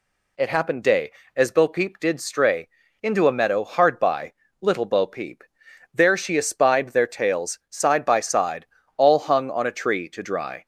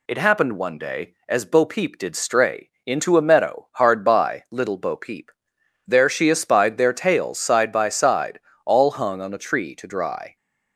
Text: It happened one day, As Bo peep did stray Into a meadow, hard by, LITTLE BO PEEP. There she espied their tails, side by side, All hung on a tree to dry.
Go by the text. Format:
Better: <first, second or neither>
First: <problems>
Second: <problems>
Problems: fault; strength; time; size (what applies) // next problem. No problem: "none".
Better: second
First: skips "one"; at 0.8 s // pauses between "stray" and "Into"; slight; at 2.6 s; 0.36 s long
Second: pauses between "stray" and "Into"; slight; at 2.6 s; 0.16 s long